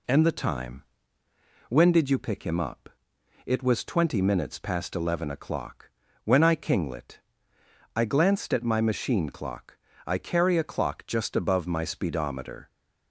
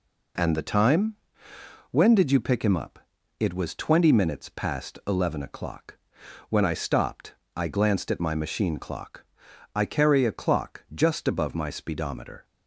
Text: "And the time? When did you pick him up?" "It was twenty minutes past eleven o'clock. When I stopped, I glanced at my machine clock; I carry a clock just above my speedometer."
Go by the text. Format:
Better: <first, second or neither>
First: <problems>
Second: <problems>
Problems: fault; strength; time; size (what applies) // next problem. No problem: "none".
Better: second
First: says "kinglet" for "stopped"; at 6.5 s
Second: none